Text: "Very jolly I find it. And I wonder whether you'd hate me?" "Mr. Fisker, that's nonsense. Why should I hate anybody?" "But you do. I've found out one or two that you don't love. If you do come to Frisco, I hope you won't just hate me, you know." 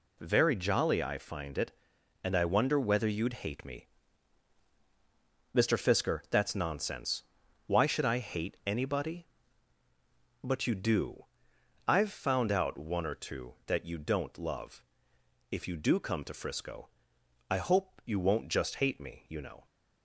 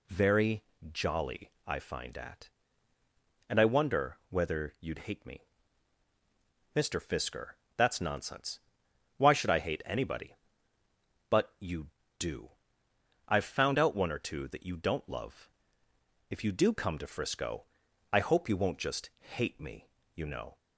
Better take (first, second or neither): first